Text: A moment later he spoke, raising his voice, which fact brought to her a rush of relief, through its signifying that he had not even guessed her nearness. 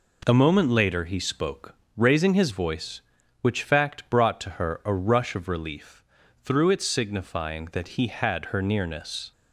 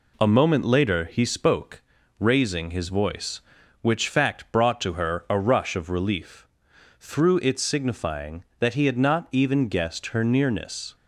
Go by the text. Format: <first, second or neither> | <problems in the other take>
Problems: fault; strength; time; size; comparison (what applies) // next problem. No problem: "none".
second | skips "not even guessed"; at 8.4 s